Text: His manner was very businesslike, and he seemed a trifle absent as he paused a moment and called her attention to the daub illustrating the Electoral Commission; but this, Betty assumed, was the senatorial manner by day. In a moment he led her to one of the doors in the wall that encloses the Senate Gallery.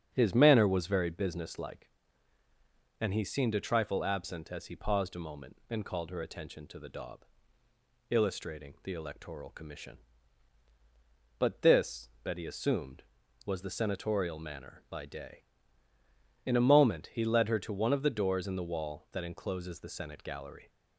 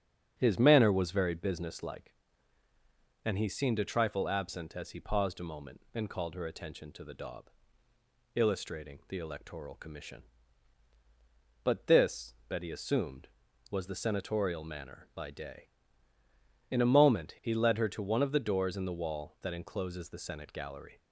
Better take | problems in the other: neither | starts louder than the rest; strong; the same in both // pauses between "daub" and "illustrating"; noticeable; the same in both

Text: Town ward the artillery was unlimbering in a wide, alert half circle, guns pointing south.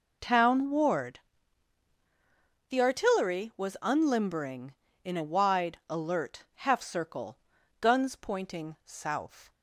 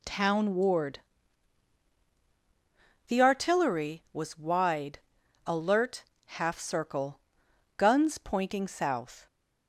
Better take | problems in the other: first | pauses between "ward" and "the"; strong; at 0.9 s; 2.1 s long; strong in the first // skips "unlimbering in a"; at 4.3 s // pauses between "alert" and "half"; slight; at 6.0 s; 0.22 s long

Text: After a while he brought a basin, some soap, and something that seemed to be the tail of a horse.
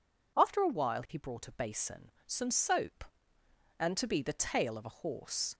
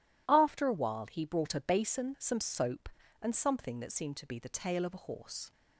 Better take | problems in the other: second | skips "something that seemed"; at 3.9 s

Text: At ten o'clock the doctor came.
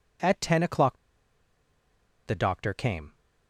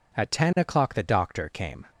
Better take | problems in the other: second | pauses between "o'clock" and "the"; strong; at 0.9 s; 1.2 s long

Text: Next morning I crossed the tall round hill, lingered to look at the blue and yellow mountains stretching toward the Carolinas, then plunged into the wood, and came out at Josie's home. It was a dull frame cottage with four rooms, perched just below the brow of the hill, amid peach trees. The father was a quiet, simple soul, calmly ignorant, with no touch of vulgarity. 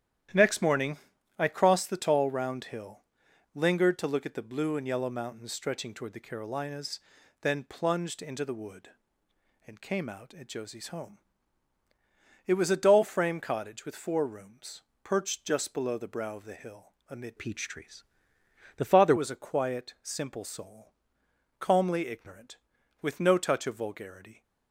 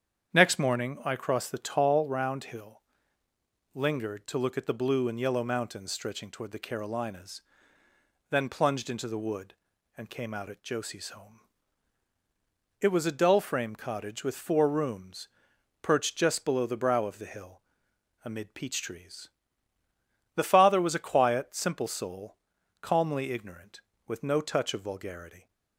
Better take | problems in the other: second | starts louder than the rest; strong; until 1.7 s; 11 dB; strong in the second // pauses between "morning" and "I"; at 0.9 s; 0.42 s long // changes voice from "peach" to "father"; from 17.3 to 19.1 s; 1.8 s long

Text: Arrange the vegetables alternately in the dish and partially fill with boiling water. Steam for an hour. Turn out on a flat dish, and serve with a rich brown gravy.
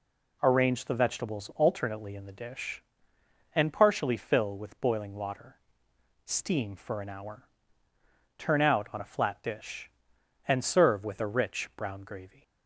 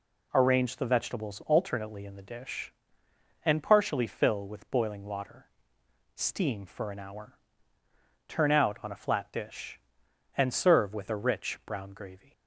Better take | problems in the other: neither | none

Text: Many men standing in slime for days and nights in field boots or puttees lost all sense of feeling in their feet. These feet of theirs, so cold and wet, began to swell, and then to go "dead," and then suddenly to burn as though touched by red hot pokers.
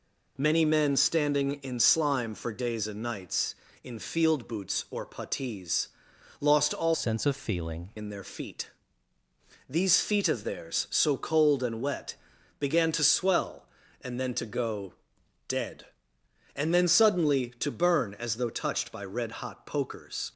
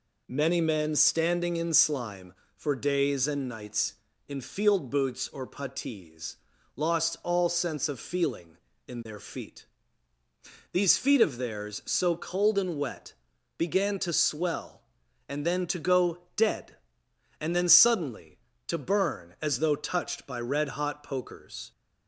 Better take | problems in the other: second | pauses between "puttees" and "lost"; noticeable; at 5.8 s; 0.54 s long; also in the second // changes voice from "sense" to "feeling"; from 6.9 to 7.9 s; 1.0 s long // pauses between "go" and "dead"; noticeable; at 14.9 s; 0.56 s long

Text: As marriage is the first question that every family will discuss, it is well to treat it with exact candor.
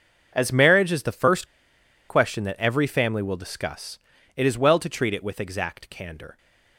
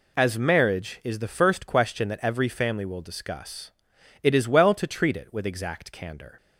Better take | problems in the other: second | pauses between "first" and "question"; noticeable; at 1.4 s; 0.62 s long

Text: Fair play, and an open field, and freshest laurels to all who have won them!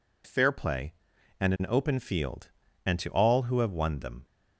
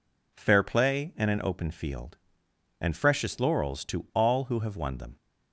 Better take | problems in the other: second | skips "freshest laurels"; at 2.9 s

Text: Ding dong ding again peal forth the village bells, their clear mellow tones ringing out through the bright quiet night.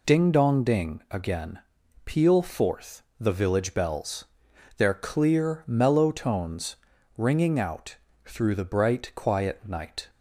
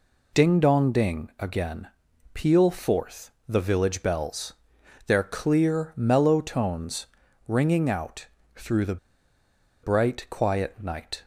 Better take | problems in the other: first | pauses between "again" and "peal"; noticeable; at 1.8 s; 0.48 s long; noticeable in the first // pauses between "forth" and "the"; slight; at 3.2 s; 0.18 s long; slight in the first // pauses between "tones" and "ringing"; at 7.0 s; 0.40 s long; also in the first // pauses between "out" and "through"; slight; at 8.2 s; 0.30 s long; slight in the first // pauses between "the" and "bright"; noticeable; at 8.9 s; 0.87 s long

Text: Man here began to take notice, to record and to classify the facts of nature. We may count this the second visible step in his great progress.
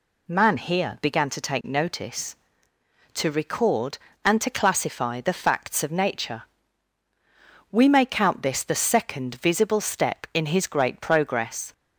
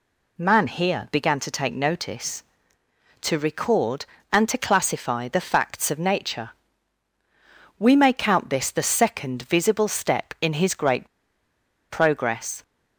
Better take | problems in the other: first | pauses between "great" and "progress"; noticeable; at 11.0 s; 0.82 s long

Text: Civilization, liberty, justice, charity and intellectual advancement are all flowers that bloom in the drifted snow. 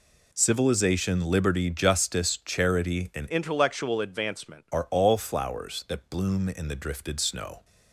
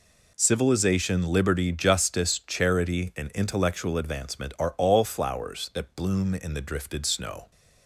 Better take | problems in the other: second | changes voice from "intellectual" to "advancement"; from 3.3 to 4.6 s; 1.3 s long

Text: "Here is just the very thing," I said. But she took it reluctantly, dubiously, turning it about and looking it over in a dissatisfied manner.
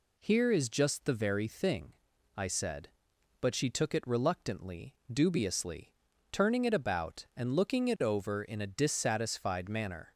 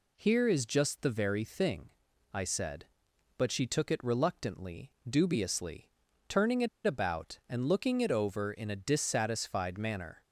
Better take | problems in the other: first | pauses between "it" and "about"; slight; at 6.6 s; 0.17 s long

